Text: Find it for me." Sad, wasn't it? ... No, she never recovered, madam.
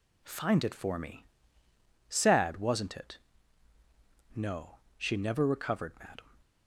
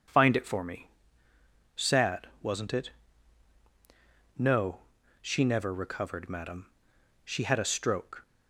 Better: first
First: none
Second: goes on to say "She had a stroke"; noticeable; from 7.2 s on; 1.0 s long

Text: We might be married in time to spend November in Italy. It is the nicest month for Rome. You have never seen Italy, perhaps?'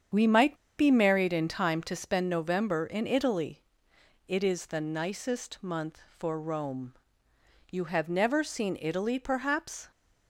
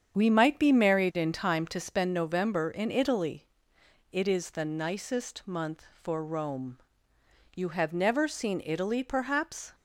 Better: second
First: starts louder than the rest; strong; until 1.3 s; 8 dB // pauses between "might" and "be"; slight; at 0.5 s; 0.23 s long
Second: starts louder than the rest; strong; until 1.2 s; 8 dB

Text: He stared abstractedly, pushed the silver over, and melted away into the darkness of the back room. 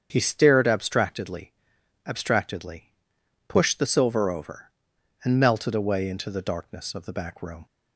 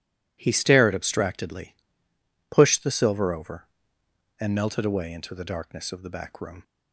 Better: second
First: starts louder than the rest; strong; until 1.1 s; 7.5 dB // says "abstractedly" twice; at 2.0 s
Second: none

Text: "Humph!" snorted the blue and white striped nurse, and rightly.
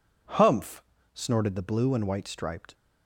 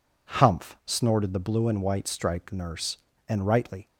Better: second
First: stops before "nurse and rightly"; at 2.7 s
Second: none

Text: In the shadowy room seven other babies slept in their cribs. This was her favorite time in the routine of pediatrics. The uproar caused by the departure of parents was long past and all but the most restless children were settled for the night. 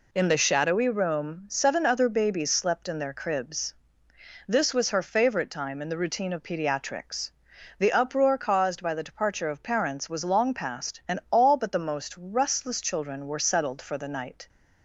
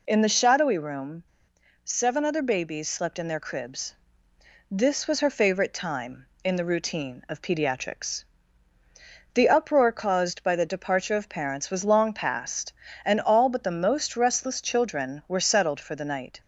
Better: first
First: none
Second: pauses between "room" and "seven"; noticeable; at 1.2 s; 0.60 s long

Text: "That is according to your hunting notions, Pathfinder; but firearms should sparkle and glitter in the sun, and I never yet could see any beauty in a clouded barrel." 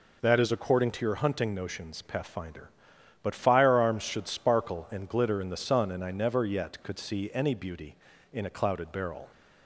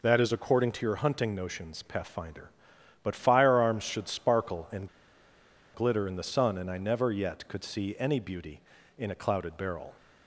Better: first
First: none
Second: pauses between "and" and "glitter"; noticeable; at 4.8 s; 0.86 s long

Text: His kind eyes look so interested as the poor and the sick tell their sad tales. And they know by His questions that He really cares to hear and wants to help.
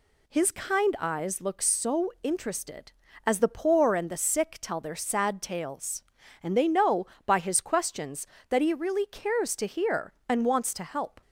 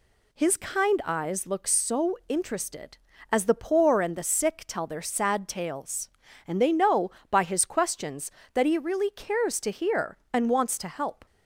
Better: neither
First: none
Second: none

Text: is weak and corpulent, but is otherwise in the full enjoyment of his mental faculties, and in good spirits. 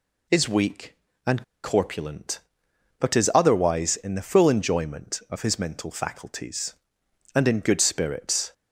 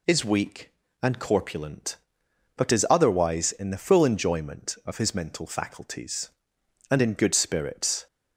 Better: second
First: pauses between "and" and "corpulent"; slight; at 1.4 s; 0.21 s long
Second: none

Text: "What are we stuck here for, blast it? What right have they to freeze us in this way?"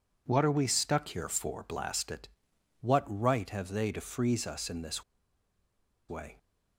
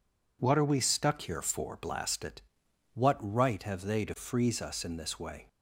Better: second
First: pauses between "this" and "way"; at 5.0 s; 1.0 s long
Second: none

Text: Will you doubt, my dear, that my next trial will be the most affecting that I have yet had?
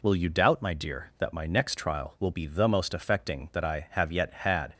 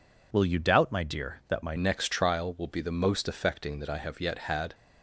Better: first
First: none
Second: changes voice at "next"; from 1.7 s on; 3.0 s long

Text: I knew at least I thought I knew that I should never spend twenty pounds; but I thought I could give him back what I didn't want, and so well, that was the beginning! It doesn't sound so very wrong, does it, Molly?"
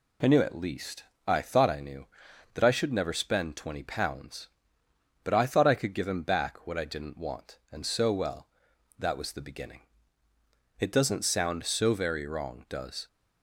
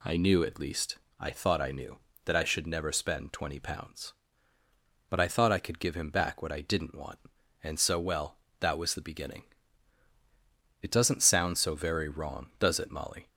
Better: second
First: pauses between "least" and "I"; slight; at 1.0 s; 0.22 s long // stops before "it Molly"; at 13.0 s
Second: pauses between "least" and "I"; slight; at 0.9 s; 0.22 s long

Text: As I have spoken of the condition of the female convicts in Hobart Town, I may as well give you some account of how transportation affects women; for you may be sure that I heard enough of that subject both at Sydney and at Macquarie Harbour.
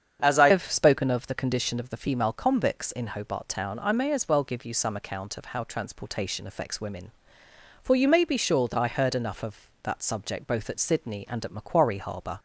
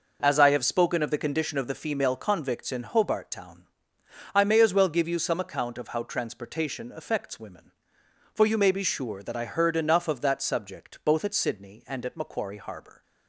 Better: second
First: starts louder than the rest; strong; until 1.2 s; 8 dB // changes voice at "have"; from 0.5 s on; 11.8 s long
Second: none

